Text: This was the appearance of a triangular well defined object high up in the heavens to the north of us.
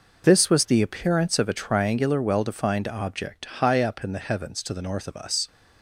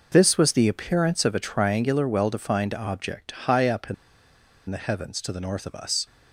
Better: first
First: pauses between "object" and "high"; slight; at 3.4 s; 0.18 s long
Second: pauses between "object" and "high"; slight; at 3.3 s; 0.18 s long // pauses between "in" and "the"; noticeable; at 3.9 s; 0.74 s long

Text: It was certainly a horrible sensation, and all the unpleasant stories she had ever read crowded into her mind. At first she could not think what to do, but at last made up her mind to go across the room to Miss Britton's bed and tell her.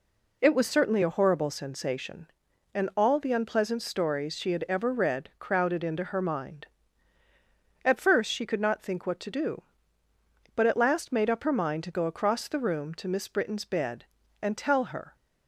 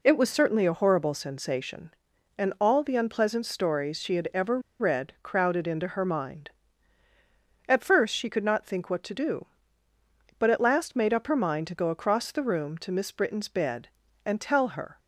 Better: first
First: none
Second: pauses between "ever" and "read"; slight; at 4.5 s; 0.20 s long

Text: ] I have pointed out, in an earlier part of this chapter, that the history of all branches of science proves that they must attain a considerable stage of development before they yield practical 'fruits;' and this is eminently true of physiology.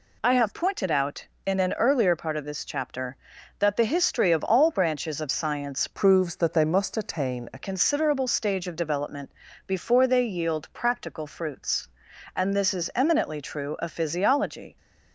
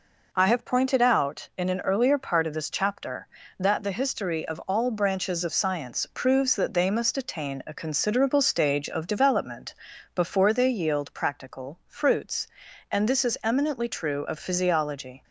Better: second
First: changes voice from "proves" to "a"; from 5.9 to 7.5 s; 1.6 s long // pauses between "development" and "before"; slight; at 9.3 s; 0.34 s long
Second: pauses between "development" and "before"; at 9.7 s; 0.40 s long

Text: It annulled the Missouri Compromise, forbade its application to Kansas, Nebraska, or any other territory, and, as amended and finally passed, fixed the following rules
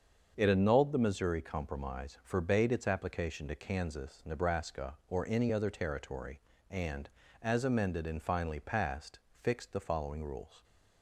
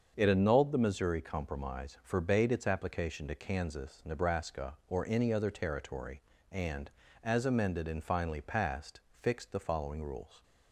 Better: neither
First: starts louder than the rest; until 1.3 s; 6.5 dB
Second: starts louder than the rest; until 1.1 s; 6.5 dB

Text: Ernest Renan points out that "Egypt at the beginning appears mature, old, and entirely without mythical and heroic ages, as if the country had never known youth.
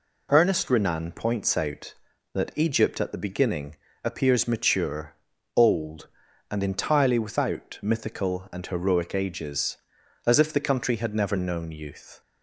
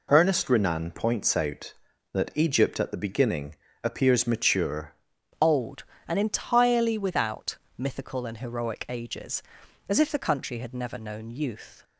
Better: first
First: pauses between "beginning" and "appears"; slight; at 3.7 s; 0.30 s long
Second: pauses between "beginning" and "appears"; slight; at 3.5 s; 0.30 s long // changes voice at "old"; from 5.4 s on; 6.4 s long // pauses between "without" and "mythical"; slight; at 7.5 s; 0.20 s long

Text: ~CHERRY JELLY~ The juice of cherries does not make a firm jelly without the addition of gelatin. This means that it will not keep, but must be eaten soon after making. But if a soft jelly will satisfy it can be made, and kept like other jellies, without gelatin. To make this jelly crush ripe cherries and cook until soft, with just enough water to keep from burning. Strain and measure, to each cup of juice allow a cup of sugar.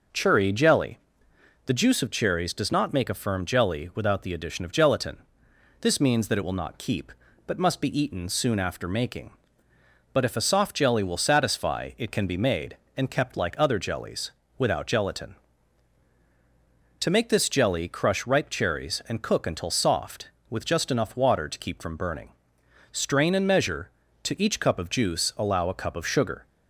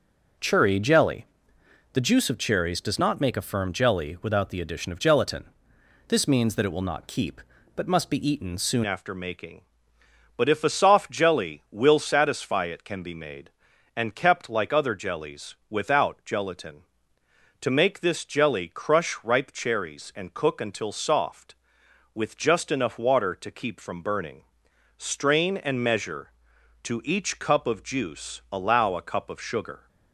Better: first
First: none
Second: changes voice at "after"; from 8.8 s on; 21.0 s long

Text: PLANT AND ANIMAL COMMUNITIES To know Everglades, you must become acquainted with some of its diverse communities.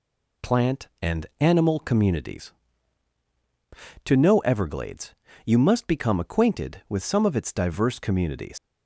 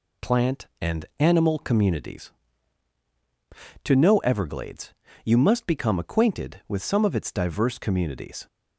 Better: second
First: leaves "communities" unfinished; at 8.5 s; 95 ms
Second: none

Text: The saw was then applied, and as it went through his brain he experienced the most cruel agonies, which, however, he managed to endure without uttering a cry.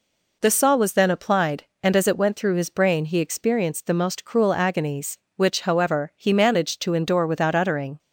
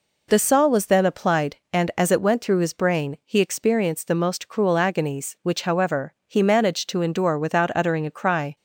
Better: second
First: stops before "a cry"; at 7.9 s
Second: none

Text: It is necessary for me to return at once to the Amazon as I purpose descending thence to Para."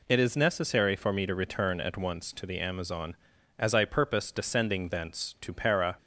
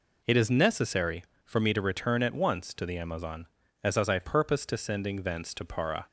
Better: first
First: none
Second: says "as" twice; at 3.9 s

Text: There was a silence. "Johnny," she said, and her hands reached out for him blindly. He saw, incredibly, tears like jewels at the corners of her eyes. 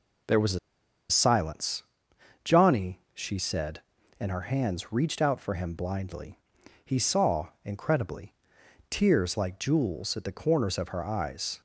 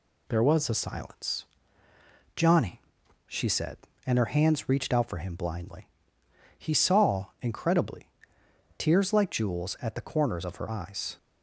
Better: second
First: pauses between "a" and "silence"; noticeable; at 0.5 s; 0.51 s long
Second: none

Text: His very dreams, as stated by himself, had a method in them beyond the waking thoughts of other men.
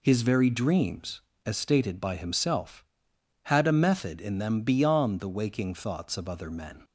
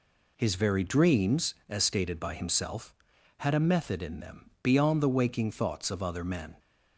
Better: neither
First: none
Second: none

